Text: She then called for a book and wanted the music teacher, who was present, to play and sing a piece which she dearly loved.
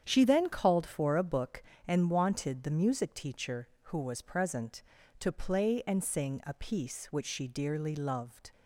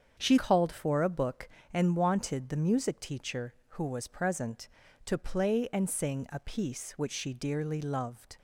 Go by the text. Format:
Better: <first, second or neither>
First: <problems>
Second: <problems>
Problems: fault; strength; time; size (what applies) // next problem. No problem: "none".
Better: first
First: starts louder than the rest; strong; until 1.0 s; 8.5 dB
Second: starts louder than the rest; strong; until 1.1 s; 7.5 dB // skips "then"; at 0.3 s